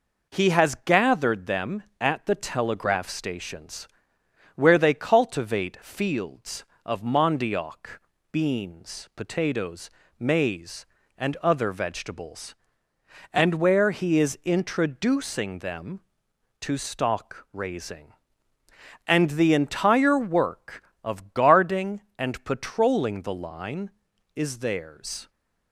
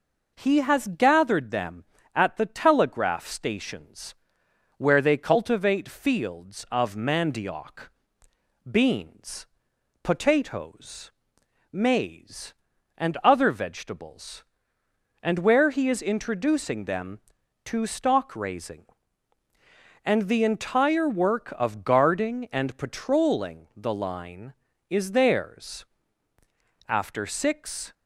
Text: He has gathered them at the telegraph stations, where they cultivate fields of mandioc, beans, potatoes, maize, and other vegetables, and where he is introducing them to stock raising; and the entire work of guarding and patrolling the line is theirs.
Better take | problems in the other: first | goes on to say "After six"; noticeable; from 26.8 s on; 1.0 s long

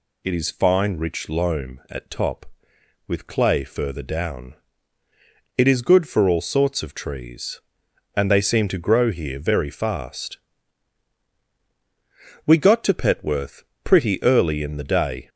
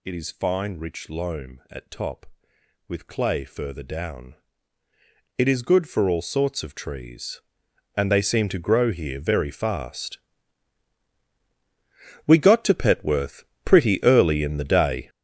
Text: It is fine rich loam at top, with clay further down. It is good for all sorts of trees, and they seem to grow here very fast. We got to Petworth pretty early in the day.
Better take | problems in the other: first | gets louder; strong; throughout; 11.5 dB // pauses between "Petworth" and "pretty"; slight; at 13.4 s; 0.22 s long; slight in the first

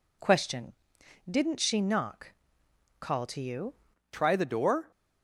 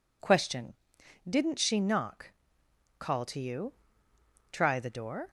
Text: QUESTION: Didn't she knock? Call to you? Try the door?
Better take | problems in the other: second | changes voice at "Try"; from 4.1 s on; 0.8 s long

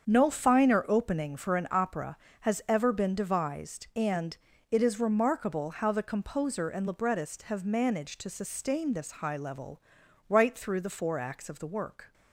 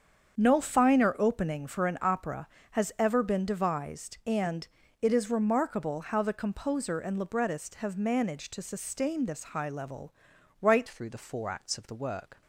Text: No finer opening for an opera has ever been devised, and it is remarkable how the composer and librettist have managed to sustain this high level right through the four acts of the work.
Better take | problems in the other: first | starts louder than the rest; strong; until 1.4 s; 7.5 dB; strong in the first // pauses between "and" and "it"; slight; at 4.6 s; 0.34 s long; slight in the first // pauses between "level" and "right"; noticeable; at 10.1 s; 0.48 s long; noticeable in the first // changes voice at "through"; from 10.8 s on; 1.6 s long

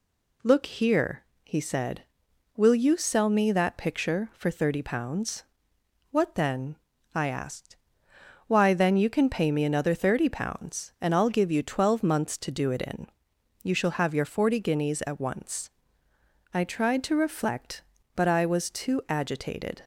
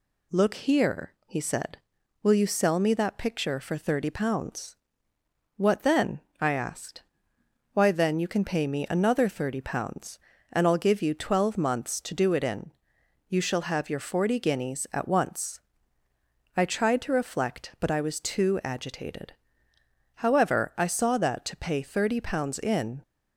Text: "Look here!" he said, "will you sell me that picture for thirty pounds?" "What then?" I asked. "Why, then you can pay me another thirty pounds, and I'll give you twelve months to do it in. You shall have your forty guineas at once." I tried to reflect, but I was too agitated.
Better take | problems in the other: first | goes on to say "However I saw that to pay thirty pounds in"; strong; from 20.1 s on; 2.8 s long

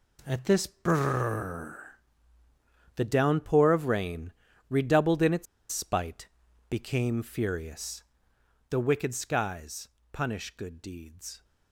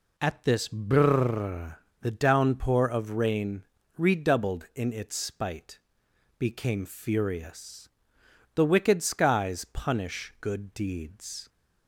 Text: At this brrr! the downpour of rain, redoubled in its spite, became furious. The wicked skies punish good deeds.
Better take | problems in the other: second | pauses between "its" and "spite"; slight; at 5.4 s; 0.26 s long // pauses between "skies" and "punish"; slight; at 9.8 s; 0.24 s long

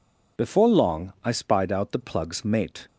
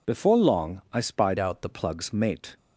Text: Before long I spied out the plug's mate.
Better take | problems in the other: first | changes voice from "out" to "the"; from 1.3 to 1.6 s; 0.3 s long

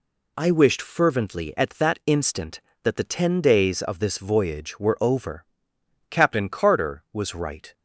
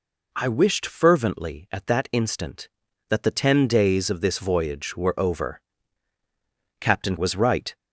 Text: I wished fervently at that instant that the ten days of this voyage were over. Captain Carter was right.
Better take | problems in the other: first | skips "Carter"; at 7.1 s

